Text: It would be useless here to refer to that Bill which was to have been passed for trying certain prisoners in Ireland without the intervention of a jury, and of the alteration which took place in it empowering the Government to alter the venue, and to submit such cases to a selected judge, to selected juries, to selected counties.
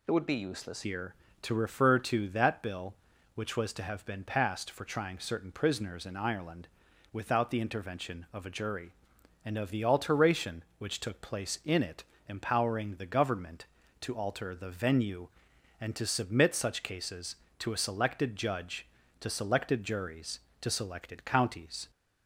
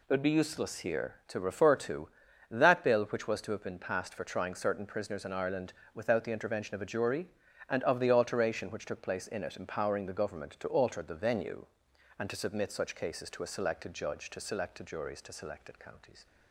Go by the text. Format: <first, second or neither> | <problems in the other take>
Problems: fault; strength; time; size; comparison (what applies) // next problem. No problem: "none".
second | changes voice at "here"; from 0.8 s on; 21.0 s long // pauses between "Ireland" and "without"; at 6.6 s; 0.44 s long; slight in the second // pauses between "it" and "empowering"; slight; at 12.0 s; 0.24 s long